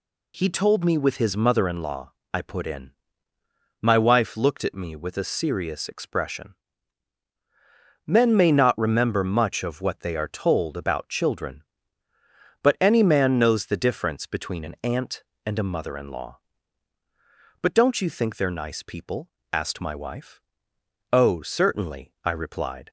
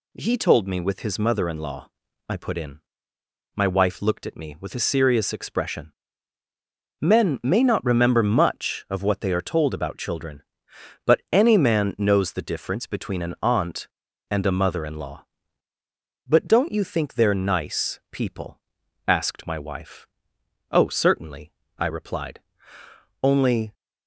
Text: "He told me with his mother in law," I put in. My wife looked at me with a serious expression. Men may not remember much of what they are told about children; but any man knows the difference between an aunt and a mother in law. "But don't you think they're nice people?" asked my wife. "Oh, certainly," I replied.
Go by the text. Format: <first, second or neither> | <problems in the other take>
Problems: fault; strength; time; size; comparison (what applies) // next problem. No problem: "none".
first | goes on to say "Only"; from 23.2 s on; 0.52 s long